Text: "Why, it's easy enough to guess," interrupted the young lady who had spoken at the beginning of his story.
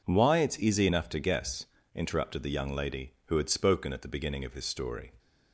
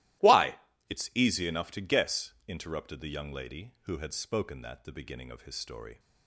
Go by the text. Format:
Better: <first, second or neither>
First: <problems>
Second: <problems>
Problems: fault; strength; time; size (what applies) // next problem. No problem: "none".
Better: first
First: none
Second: starts louder than the rest; strong; until 1.5 s; 16 dB // says "that" for "at"; at 4.6 s